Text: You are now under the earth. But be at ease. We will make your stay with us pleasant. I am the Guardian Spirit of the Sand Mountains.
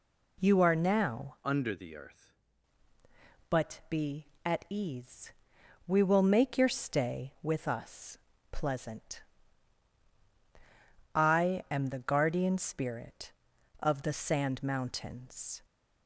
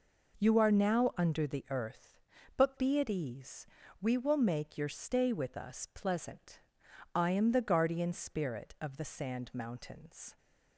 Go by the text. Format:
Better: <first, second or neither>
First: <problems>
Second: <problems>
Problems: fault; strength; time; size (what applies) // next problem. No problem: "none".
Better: second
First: changes voice from "under" to "earth"; from 1.4 to 2.3 s; 0.9 s long // pauses between "us" and "pleasant"; slight; at 8.1 s; 0.34 s long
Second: none